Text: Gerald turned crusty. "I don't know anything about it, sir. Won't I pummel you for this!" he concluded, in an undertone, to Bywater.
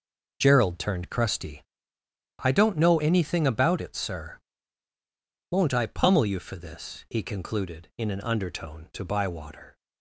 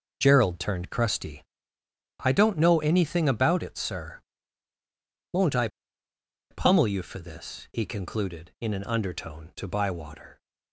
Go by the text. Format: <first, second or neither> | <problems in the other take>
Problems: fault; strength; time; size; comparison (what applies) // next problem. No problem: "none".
first | pauses between "I" and "pummel"; noticeable; at 5.6 s; 0.83 s long